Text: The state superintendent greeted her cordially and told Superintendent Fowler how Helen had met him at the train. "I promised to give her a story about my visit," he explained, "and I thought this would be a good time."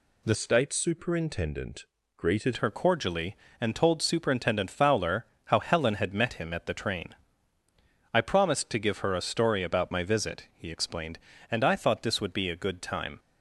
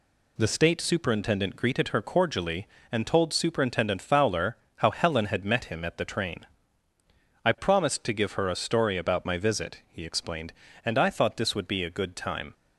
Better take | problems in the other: second | changes voice from "state" to "greeted"; from 0.3 to 2.5 s; 2.2 s long // pauses between "superintendent" and "greeted"; slight; at 1.8 s; 0.30 s long // pauses between "Fowler" and "how"; slight; at 5.2 s; 0.18 s long; slight in the second

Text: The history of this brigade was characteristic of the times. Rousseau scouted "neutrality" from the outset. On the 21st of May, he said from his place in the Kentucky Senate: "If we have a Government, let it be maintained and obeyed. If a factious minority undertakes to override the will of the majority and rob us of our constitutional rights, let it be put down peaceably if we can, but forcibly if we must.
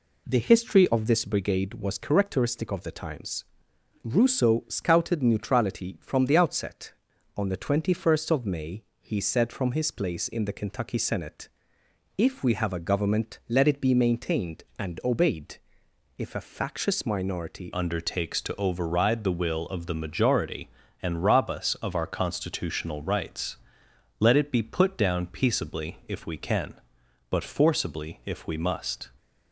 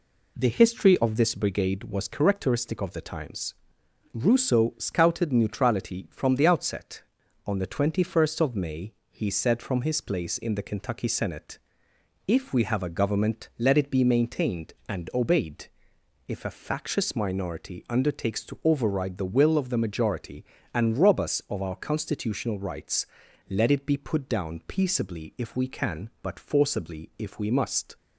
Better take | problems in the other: second | changes voice at "undertakes"; from 17.7 s on; 11.3 s long

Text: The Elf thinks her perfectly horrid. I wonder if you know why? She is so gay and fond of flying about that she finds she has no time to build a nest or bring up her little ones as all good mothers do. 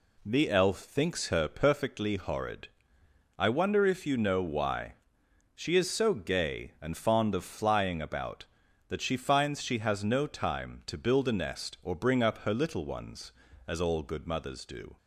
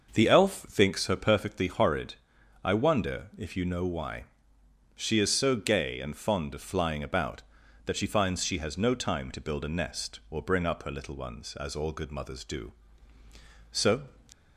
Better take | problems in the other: first | starts louder than the rest; until 1.1 s; 6 dB // goes on to say "So"; slight; from 13.7 s on; 0.32 s long

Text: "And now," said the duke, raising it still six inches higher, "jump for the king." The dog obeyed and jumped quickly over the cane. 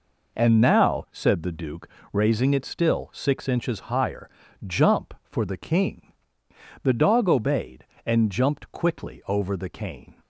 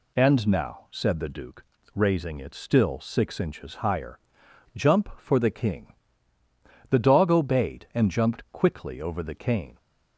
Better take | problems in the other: neither | none

